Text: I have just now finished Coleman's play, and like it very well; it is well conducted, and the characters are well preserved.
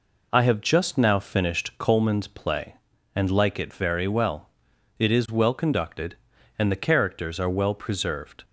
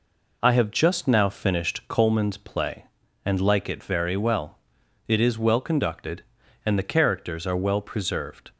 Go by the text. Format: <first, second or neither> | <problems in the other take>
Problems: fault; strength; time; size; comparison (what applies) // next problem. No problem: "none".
neither | none